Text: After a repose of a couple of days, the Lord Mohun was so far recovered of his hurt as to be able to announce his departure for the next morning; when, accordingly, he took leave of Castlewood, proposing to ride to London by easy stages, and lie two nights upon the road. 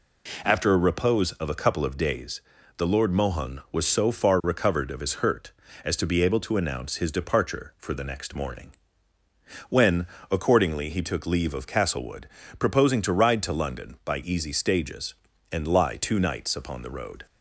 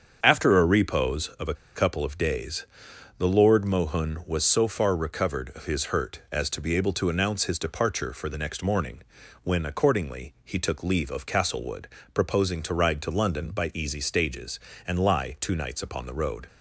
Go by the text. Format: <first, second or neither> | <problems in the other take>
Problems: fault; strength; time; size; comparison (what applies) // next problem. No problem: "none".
first | starts louder than the rest; strong; until 1.2 s; 7.5 dB // pauses between "a" and "couple"; slight; at 1.5 s; 0.21 s long